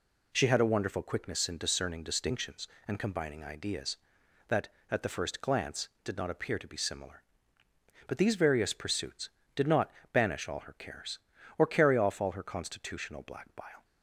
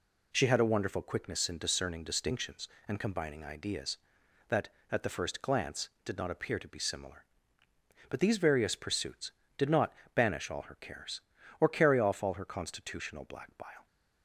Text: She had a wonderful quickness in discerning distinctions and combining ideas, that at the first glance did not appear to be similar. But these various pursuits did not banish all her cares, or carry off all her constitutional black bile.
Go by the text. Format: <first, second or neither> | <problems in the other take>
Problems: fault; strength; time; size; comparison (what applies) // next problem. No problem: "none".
neither | pauses between "not" and "banish"; slight; the same in both